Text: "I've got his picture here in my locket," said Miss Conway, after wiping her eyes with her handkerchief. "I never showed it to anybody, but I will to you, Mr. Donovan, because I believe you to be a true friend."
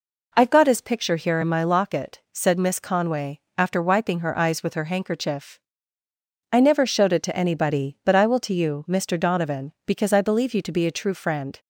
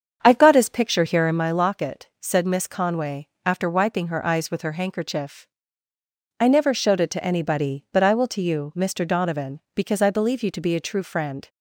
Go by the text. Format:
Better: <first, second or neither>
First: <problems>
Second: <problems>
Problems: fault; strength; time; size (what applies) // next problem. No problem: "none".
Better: first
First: none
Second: starts louder than the rest; strong; until 1.4 s; 7.5 dB